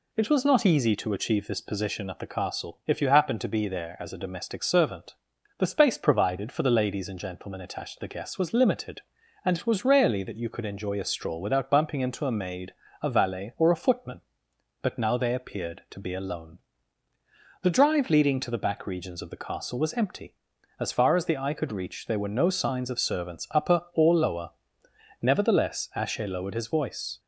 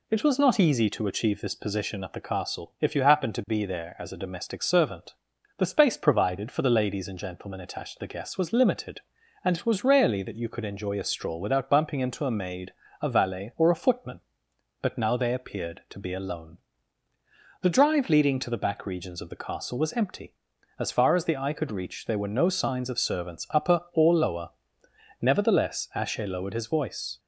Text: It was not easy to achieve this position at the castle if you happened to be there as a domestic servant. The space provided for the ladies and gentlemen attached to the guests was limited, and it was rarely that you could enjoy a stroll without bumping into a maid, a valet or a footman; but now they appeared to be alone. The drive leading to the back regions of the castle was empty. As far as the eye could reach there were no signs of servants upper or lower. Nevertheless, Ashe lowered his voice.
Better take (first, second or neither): neither